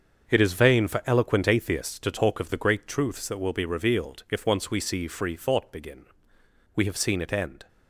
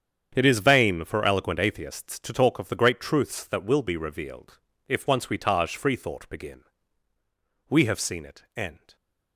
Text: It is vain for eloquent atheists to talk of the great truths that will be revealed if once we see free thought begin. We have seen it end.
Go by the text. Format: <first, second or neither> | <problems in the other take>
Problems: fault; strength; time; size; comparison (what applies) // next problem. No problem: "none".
first | starts louder than the rest; strong; until 1.3 s; 8 dB; also in the first // pauses between "revealed" and "if"; slight; at 4.5 s; 0.30 s long // says "taj" for "see"; at 5.3 s